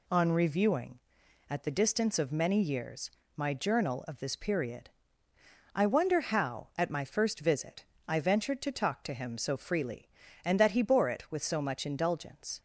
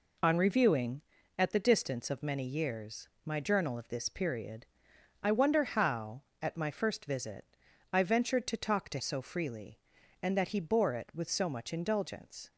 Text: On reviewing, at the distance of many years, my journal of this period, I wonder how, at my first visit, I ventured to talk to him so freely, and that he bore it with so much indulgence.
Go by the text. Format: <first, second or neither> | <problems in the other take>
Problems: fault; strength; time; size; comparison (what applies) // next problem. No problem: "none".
first | skips "him"; at 8.9 s